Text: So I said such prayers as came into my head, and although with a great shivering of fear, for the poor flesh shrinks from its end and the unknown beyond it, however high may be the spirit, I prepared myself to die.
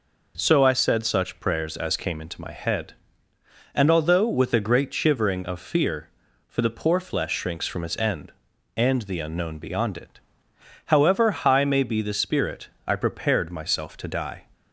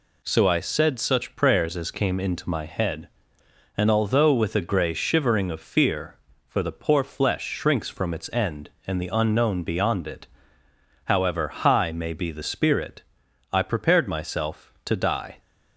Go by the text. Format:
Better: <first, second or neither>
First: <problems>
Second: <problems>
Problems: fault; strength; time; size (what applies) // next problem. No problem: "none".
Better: first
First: none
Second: says "grey" for "great"; at 4.6 s